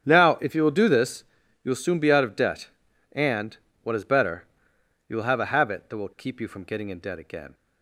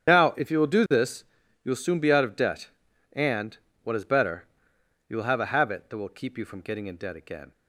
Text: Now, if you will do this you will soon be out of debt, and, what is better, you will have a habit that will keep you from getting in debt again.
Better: first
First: starts louder than the rest; strong; until 1.0 s; 9 dB // pauses between "this" and "you"; at 1.2 s; 0.40 s long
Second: loses the start of "Now"; at 0.0 s; 70 ms // starts louder than the rest; strong; until 1.1 s; 9 dB // pauses between "this" and "you"; at 1.2 s; 0.40 s long

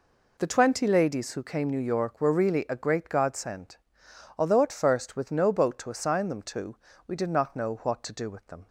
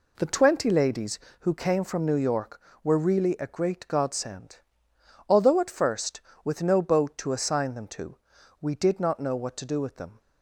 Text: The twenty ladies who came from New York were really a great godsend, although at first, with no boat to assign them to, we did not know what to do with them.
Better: second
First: skips "from"; at 1.6 s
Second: none

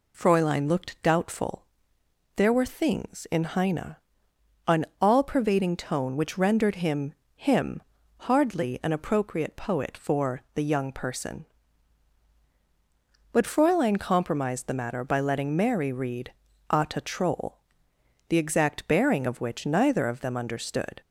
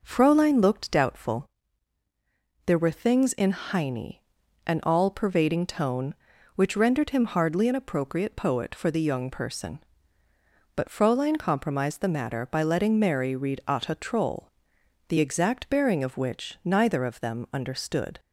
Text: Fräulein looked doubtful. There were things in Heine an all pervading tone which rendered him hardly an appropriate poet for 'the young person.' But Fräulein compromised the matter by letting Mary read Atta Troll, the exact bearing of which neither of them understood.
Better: second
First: pauses between "Heine" and "an"; noticeable; at 3.9 s; 0.70 s long // says "him" twice; at 7.3 s // pauses between "read" and "Atta"; at 16.3 s; 0.40 s long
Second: pauses between "Heine" and "an"; noticeable; at 4.1 s; 0.46 s long

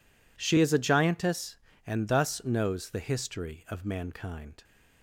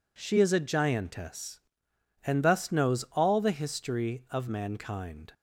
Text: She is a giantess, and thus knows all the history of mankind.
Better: second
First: skips "all"; at 2.8 s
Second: none

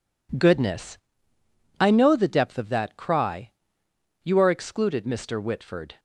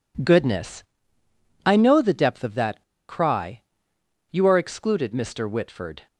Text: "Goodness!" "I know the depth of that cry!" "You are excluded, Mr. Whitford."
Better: first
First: none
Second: pauses between "that" and "cry"; slight; at 2.8 s; 0.27 s long

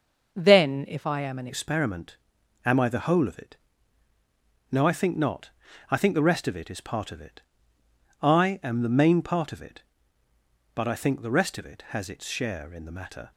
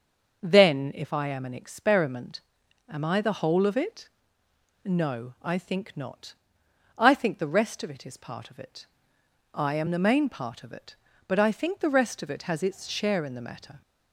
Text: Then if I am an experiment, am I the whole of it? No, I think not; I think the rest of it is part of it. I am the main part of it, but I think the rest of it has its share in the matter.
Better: second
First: starts louder than the rest; until 1.3 s; 6 dB // changes voice at "experiment"; from 1.4 s on; 11.9 s long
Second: starts louder than the rest; until 1.4 s; 6.5 dB

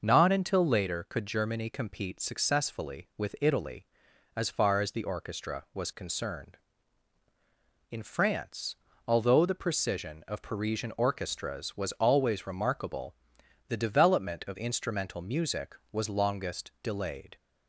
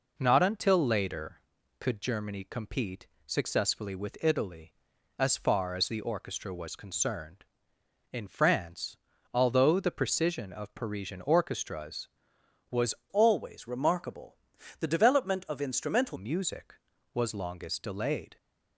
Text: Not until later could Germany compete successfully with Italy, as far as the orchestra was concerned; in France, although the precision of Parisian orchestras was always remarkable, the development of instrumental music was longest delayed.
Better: first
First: none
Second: pauses between "compete" and "successfully"; slight; at 3.0 s; 0.20 s long // changes voice from "always" to "instrumental"; from 13.0 to 16.1 s; 3.1 s long

